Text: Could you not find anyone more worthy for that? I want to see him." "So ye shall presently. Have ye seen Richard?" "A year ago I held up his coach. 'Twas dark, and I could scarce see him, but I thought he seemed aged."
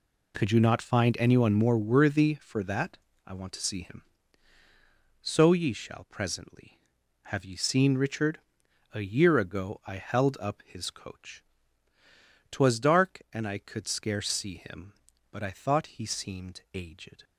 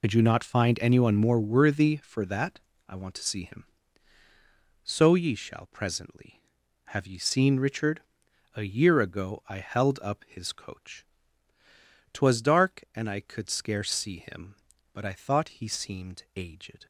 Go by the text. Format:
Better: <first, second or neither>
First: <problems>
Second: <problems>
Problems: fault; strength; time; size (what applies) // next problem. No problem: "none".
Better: first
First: none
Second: loses the start of "Could"; at 0.0 s; 70 ms